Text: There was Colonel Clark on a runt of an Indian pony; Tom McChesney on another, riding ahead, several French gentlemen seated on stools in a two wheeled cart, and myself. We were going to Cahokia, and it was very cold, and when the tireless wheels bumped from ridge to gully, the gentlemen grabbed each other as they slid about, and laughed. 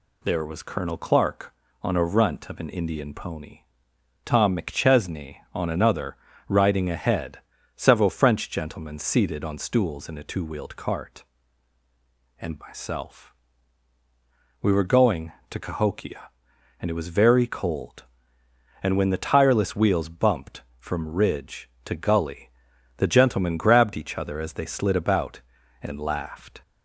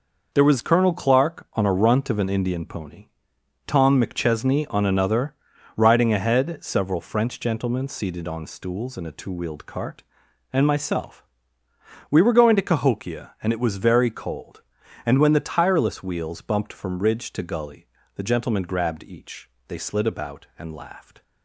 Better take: first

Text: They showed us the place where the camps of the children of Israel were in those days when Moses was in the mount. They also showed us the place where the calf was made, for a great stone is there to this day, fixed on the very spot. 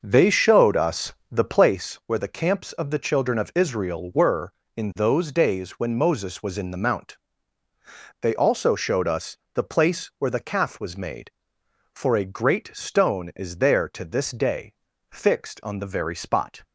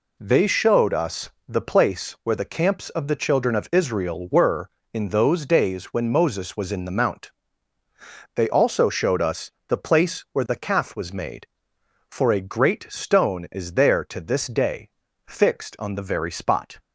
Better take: second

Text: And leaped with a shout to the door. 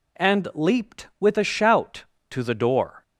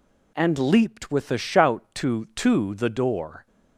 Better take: first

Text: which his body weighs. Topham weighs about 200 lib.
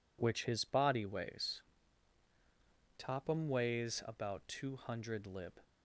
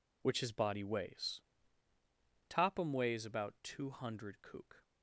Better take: first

